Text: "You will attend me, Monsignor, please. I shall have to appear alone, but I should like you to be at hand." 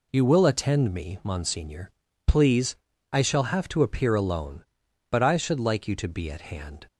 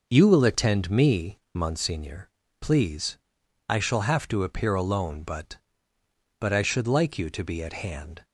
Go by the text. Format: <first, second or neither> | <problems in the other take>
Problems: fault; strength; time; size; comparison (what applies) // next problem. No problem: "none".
first | says "but" twice; at 6.4 s